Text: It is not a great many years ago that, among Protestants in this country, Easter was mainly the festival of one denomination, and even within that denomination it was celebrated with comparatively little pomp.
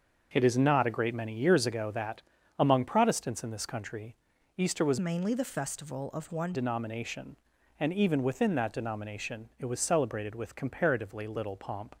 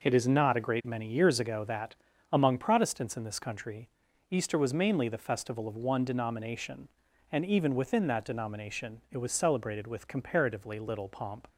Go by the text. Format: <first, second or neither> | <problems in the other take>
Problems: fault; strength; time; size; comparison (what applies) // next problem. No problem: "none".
second | starts louder than the rest; until 1.3 s; 6.5 dB // changes voice from "mainly" to "one"; from 4.9 to 6.5 s; 1.6 s long